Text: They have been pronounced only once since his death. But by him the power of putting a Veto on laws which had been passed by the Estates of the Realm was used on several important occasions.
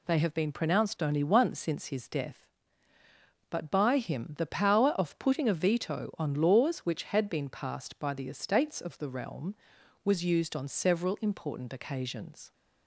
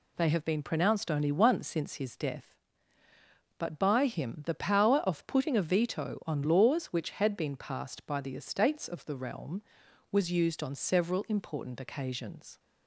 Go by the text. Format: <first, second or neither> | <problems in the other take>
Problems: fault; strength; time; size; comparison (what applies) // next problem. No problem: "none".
neither | none